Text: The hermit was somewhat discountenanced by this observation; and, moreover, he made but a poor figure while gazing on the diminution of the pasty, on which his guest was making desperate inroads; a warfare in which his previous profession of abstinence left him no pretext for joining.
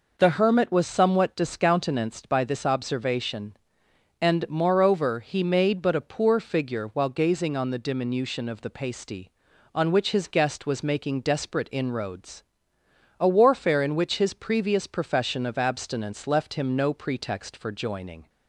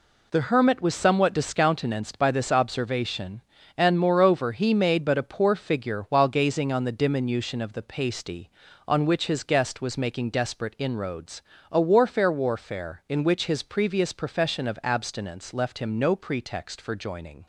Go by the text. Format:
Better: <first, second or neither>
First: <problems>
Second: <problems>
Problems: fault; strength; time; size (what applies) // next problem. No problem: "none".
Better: first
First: none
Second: says "warfare" twice; at 12.2 s